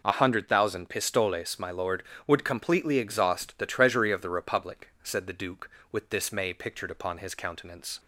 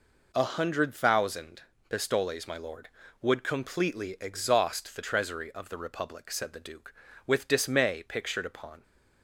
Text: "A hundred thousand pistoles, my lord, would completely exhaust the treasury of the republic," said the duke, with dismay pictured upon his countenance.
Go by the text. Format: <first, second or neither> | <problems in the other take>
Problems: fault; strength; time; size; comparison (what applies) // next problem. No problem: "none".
first | pauses between "thousand" and "pistoles"; slight; at 1.6 s; 0.26 s long // stops before "his countenance"; at 8.8 s